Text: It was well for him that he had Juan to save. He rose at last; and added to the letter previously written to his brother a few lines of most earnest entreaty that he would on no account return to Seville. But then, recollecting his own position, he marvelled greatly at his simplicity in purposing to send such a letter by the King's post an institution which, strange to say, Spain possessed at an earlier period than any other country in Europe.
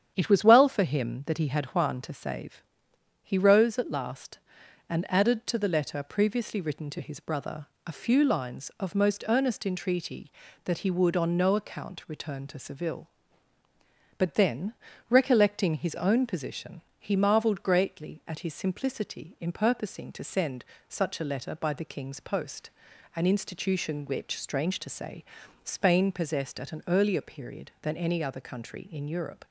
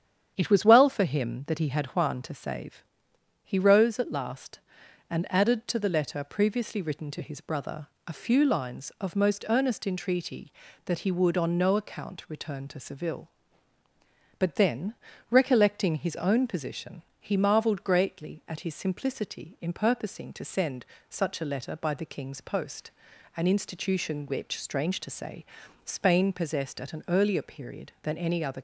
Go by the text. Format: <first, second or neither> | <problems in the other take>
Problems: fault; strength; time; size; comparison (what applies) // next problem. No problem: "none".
first | starts louder than the rest; strong; until 1.3 s; 9 dB; strong in the first // pauses between "brother" and "a"; slight; at 7.8 s; 0.18 s long; slight in the first // pauses between "send" and "such"; slight; at 20.8 s; 0.24 s long; slight in the first // pauses between "post" and "an"; noticeable; at 22.8 s; 0.48 s long; noticeable in the first // stops before "country in Europe"; at 28.5 s